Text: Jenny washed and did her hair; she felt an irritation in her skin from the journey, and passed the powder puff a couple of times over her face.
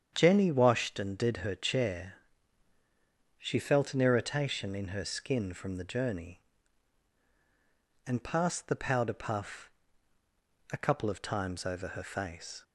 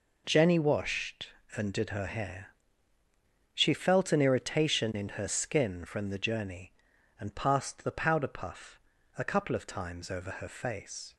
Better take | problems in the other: second | starts louder than the rest; strong; until 1.1 s; 8 dB // says "chair" for "hair"; at 1.5 s // pauses between "puff" and "a"; at 9.7 s; 1.0 s long; also in the second

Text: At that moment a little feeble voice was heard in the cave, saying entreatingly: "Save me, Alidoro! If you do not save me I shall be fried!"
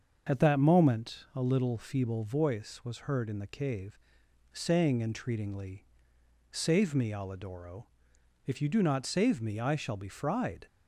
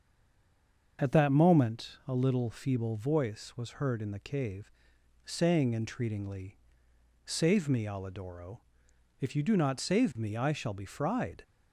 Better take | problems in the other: first | stays silent before the first word; slight; until 0.9 s; 0.9 s long // starts louder than the rest; until 2.0 s; 6.5 dB; also in the first

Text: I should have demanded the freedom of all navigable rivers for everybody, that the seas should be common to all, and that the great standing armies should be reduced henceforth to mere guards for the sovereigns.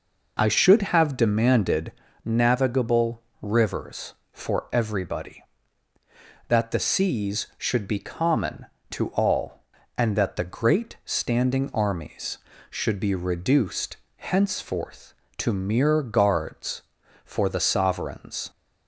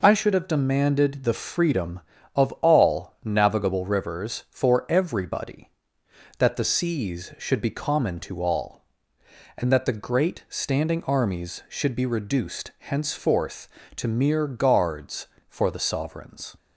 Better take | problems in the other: second | skips "the freedom of all"; at 2.0 s // pauses between "navigable" and "rivers"; slight; at 3.2 s; 0.18 s long // pauses between "reduced" and "henceforth"; slight; at 13.9 s; 0.20 s long

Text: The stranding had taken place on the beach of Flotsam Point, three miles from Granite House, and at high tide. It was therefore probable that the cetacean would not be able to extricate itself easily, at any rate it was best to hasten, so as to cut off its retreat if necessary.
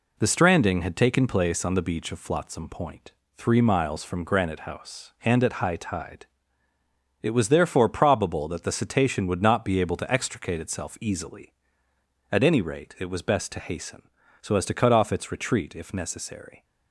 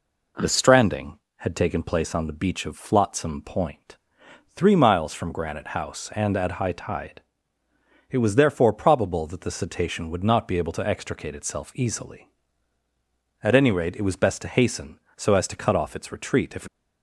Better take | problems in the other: first | stops before "necessary"; at 16.6 s

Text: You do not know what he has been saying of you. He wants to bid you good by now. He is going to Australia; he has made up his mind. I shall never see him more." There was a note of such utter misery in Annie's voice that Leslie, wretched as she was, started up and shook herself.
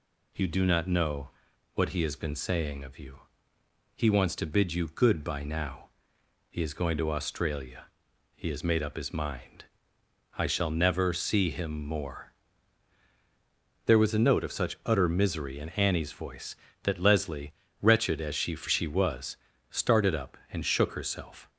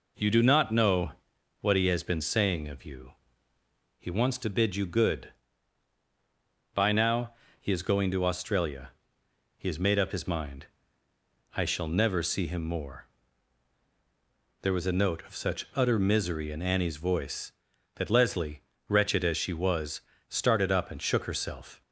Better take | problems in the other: second | pauses between "know" and "what"; noticeable; at 1.2 s; 0.46 s long; noticeable in the second // says "she" twice; at 18.5 s

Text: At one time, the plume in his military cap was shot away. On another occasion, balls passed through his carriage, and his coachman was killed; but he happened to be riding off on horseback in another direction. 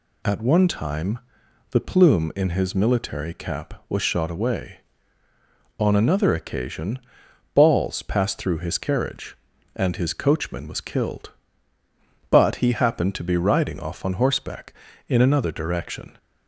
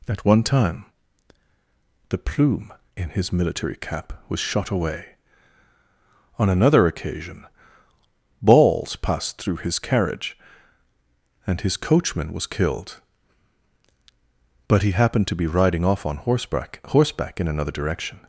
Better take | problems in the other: first | says "horseback" twice; at 16.8 s

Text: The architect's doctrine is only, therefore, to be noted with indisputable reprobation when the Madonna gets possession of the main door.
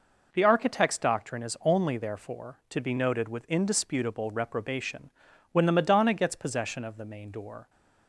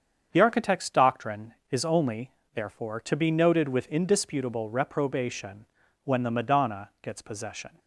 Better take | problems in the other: first | starts louder than the rest; strong; until 1.3 s; 7.5 dB // pauses between "reprobation" and "when"; at 5.6 s; 0.40 s long; also in the first // stops before "of the main door"; at 7.7 s

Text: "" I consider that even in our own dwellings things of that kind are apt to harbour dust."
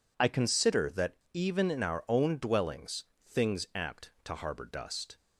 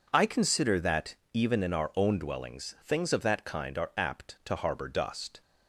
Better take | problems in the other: second | pauses between "that" and "even"; slight; at 1.1 s; 0.15 s long; slight in the second // pauses between "dwellings" and "things"; slight; at 3.0 s; 0.24 s long // skips "of that kind are"; at 3.7 s

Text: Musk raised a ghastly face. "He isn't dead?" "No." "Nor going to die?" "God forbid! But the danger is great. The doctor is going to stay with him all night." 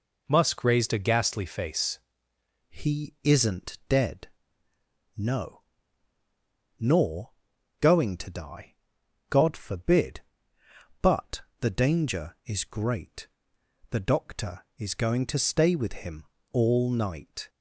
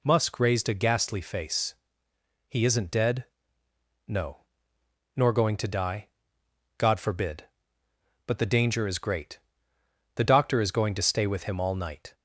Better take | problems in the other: second | changes voice at "He"; from 2.6 s on; 14.8 s long // pauses between "Nor" and "going"; noticeable; at 7.3 s; 0.50 s long // pauses between "But" and "the"; slight; at 11.4 s; 0.20 s long // pauses between "him" and "all"; slight; at 16.2 s; 0.26 s long

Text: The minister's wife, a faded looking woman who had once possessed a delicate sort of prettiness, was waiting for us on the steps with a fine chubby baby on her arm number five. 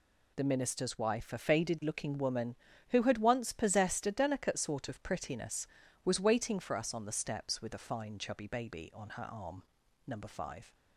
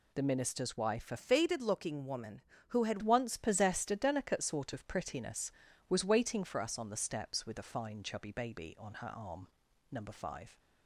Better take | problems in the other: first | changes voice from "faded" to "had"; from 1.1 to 2.9 s; 1.8 s long // pauses between "arm" and "number"; at 9.4 s; 0.44 s long; also in the first

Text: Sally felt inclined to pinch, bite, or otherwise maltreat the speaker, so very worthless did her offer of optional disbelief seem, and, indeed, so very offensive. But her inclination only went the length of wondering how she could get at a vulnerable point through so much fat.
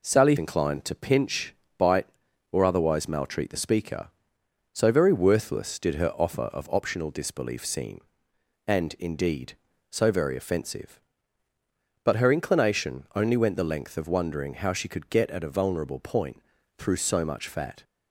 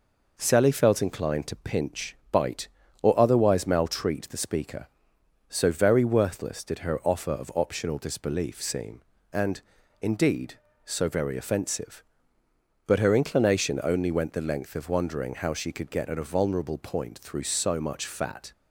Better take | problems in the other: second | skips "felt"; at 0.3 s // pauses between "point" and "through"; at 16.3 s; 0.38 s long

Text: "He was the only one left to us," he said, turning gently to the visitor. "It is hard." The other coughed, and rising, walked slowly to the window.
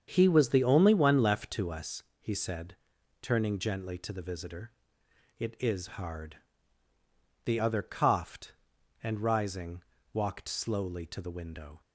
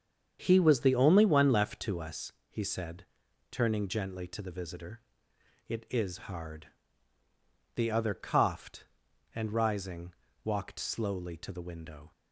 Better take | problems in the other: neither | starts louder than the rest; strong; the same in both

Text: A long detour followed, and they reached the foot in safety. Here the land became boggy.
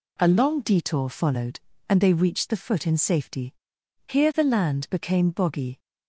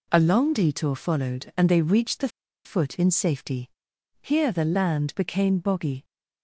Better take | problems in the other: first | pauses between "the" and "foot"; slight; at 2.2 s; 0.35 s long

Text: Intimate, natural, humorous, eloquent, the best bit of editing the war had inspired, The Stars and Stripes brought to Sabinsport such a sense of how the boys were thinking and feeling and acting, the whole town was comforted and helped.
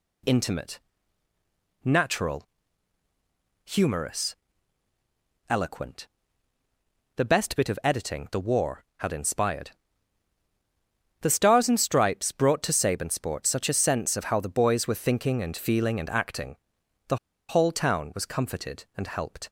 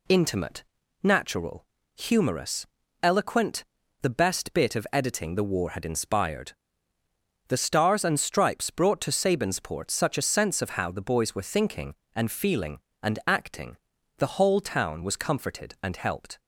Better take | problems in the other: second | pauses between "the" and "whole"; slight; at 17.1 s; 0.32 s long

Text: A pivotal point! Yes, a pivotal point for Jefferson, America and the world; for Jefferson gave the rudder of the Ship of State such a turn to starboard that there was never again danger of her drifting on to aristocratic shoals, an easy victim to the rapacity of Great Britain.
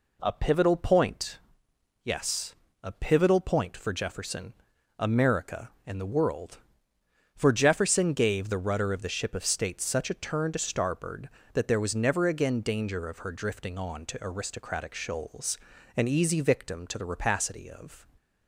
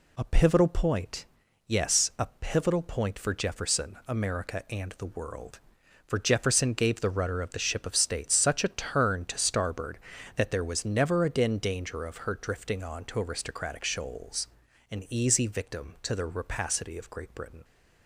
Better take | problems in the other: second | stops before "Great Britain"; at 18.1 s

